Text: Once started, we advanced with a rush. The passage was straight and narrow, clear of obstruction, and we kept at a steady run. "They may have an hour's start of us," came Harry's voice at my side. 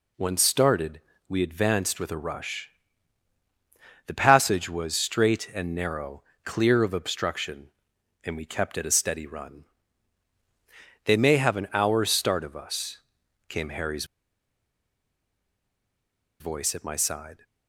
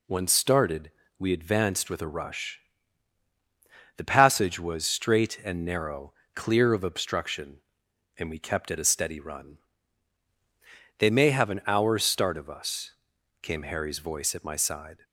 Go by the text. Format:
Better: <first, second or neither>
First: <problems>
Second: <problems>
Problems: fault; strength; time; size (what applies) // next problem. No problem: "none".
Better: second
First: pauses between "Harry's" and "voice"; strong; at 14.0 s; 2.3 s long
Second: none